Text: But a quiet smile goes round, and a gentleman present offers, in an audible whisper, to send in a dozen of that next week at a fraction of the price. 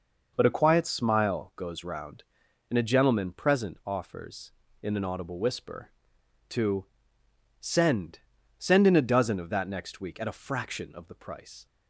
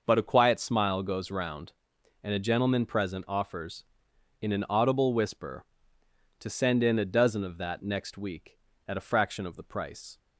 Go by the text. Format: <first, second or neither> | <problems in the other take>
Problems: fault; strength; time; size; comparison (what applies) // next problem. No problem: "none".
second | pauses between "to" and "send"; noticeable; at 6.8 s; 0.74 s long // says "send" twice; at 8.5 s